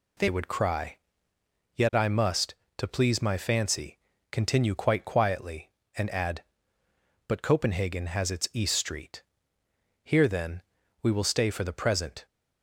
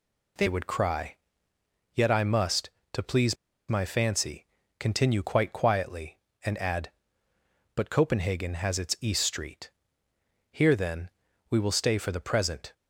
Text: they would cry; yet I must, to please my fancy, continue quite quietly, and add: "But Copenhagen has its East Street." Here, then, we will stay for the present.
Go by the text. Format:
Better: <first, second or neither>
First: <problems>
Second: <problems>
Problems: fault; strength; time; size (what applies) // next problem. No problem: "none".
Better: first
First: none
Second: pauses between "please" and "my"; slight; at 3.3 s; 0.33 s long